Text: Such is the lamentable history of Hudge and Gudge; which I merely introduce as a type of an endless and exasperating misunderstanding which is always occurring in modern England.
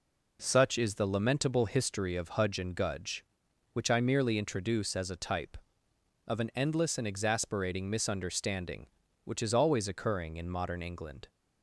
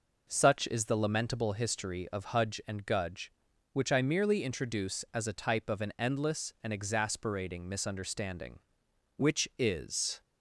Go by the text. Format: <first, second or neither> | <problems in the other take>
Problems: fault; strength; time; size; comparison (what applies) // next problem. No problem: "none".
first | stops before "always occurring in modern England"; at 10.2 s